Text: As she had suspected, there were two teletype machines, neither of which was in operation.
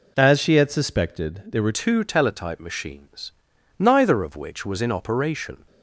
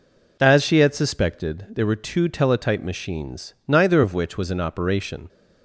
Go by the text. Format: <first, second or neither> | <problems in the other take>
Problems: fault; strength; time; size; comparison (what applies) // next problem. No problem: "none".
second | changes voice at "two"; from 1.7 s on; 3.9 s long